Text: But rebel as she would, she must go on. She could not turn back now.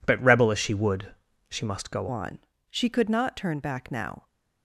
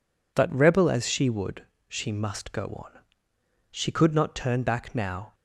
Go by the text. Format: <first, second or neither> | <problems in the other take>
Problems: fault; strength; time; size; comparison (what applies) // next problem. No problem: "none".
second | changes voice at "on"; from 2.0 s on; 2.2 s long